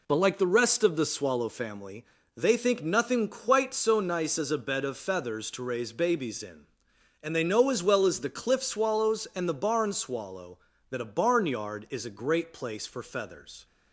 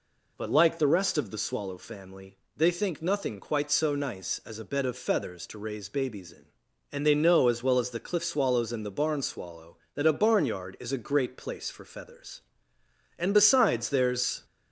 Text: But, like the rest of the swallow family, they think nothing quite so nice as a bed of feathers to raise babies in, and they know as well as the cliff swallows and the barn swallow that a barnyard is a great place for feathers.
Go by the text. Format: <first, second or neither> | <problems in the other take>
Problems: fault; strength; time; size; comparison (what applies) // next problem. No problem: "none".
first | goes on to say "And besides there's"; noticeable; from 13.1 s on; 1.2 s long